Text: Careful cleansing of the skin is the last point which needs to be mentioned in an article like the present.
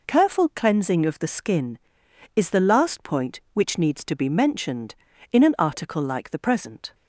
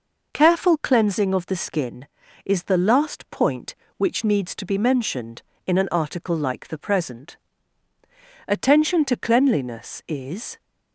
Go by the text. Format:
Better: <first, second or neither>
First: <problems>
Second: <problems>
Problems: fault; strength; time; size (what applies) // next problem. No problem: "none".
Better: first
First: none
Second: goes on to say "Attention to cleanliness is"; strong; from 8.4 s on; 2.1 s long